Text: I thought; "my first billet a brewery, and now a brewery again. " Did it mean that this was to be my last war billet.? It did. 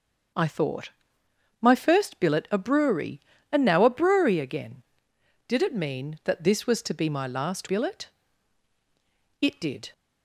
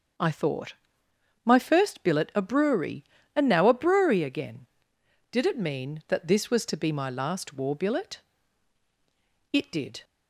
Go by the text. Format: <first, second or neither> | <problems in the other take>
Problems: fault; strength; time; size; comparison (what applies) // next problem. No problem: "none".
second | starts louder than the rest; until 2.0 s; 7 dB; strong in the second // skips "war"; at 7.6 s